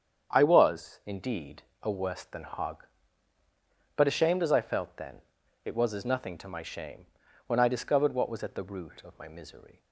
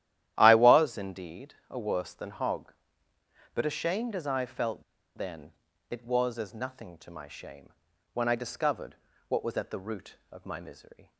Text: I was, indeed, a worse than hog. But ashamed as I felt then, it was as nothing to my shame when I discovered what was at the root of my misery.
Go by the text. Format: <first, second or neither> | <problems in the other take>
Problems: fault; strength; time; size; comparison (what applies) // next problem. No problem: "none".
first | starts louder than the rest; strong; until 1.3 s; 12.5 dB; strong in the first // pauses between "felt" and "then"; slight; at 4.8 s; 0.34 s long // pauses between "shame" and "when"; at 7.6 s; 0.44 s long; also in the first // pauses between "discovered" and "what"; slight; at 8.9 s; 0.32 s long